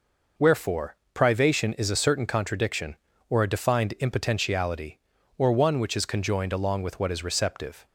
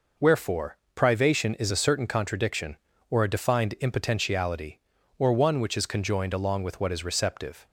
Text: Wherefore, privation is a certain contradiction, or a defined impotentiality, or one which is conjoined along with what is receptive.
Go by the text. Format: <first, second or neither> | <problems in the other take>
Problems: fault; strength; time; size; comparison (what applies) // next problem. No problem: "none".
neither | none